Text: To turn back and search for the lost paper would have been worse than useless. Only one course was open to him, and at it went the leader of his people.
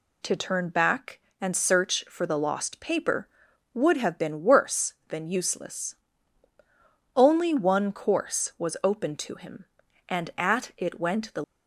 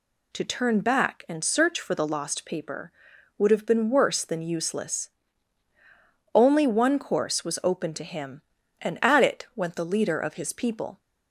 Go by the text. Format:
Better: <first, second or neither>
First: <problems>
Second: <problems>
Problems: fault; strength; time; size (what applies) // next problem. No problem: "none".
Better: second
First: stops before "leader of his people"; at 11.4 s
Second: none